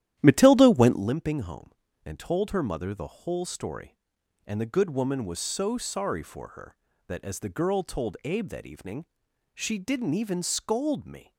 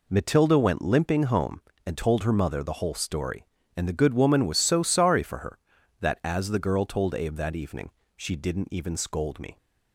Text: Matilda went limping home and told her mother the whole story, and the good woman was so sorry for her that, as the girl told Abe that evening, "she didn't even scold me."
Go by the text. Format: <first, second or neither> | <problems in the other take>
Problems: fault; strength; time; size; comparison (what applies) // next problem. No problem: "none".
second | starts louder than the rest; strong; until 1.1 s; 12 dB